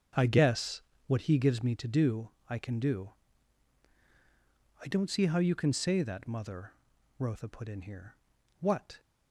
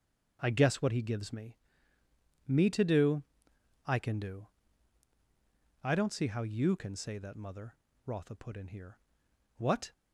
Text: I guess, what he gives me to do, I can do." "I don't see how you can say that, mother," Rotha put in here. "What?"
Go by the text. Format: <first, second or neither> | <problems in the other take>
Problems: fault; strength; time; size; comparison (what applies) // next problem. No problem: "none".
first | starts louder than the rest; until 1.4 s; 6.5 dB; also in the first // says "me" twice; at 2.4 s